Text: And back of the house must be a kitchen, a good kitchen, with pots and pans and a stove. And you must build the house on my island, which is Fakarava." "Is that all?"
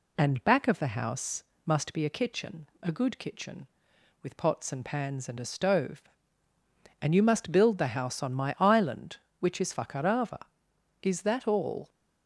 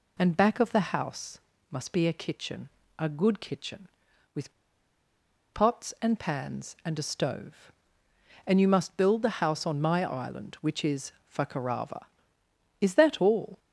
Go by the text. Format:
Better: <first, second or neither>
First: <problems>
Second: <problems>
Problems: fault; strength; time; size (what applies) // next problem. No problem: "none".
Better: first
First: pauses between "house" and "must"; slight; at 1.4 s; 0.22 s long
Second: pauses between "house" and "must"; slight; at 1.3 s; 0.32 s long // pauses between "with" and "pots"; at 4.5 s; 1.0 s long // pauses between "is" and "Fakarava"; slight; at 11.1 s; 0.18 s long